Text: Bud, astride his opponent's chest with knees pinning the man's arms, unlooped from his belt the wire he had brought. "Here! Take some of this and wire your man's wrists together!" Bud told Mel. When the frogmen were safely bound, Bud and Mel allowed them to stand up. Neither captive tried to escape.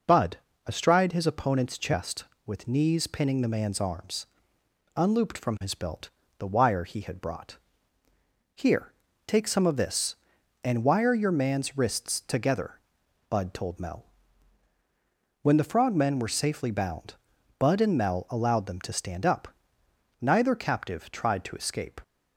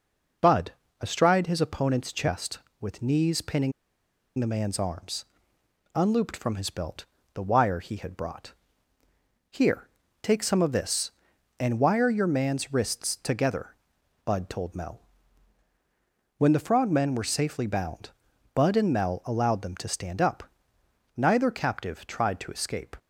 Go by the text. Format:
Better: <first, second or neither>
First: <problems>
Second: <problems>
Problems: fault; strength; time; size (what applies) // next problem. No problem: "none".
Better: first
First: pauses between "belt" and "the"; slight; at 6.0 s; 0.28 s long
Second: pauses between "pinning" and "the"; noticeable; at 3.7 s; 0.67 s long // pauses between "belt" and "the"; slight; at 7.0 s; 0.28 s long